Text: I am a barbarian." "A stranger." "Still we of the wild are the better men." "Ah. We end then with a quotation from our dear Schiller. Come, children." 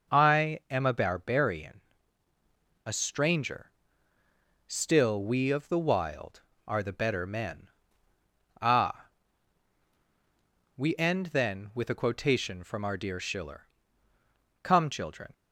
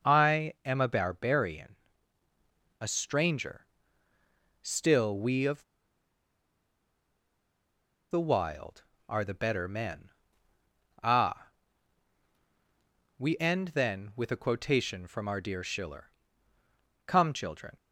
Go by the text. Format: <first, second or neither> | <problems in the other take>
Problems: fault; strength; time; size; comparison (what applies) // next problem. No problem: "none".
first | starts louder than the rest; noticeable; until 1.1 s; 6 dB; noticeable in the first // pauses between "of" and "the"; strong; at 5.6 s; 2.4 s long